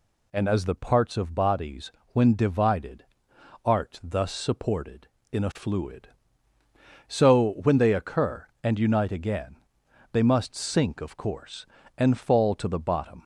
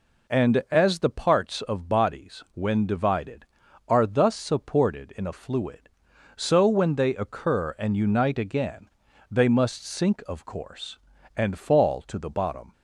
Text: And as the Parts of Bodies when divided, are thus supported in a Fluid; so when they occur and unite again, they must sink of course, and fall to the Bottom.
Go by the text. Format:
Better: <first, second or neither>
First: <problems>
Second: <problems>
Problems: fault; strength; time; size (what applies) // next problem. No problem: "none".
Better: second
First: pauses between "Bodies" and "when"; slight; at 1.8 s; 0.22 s long // says "art" for "are"; at 3.6 s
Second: none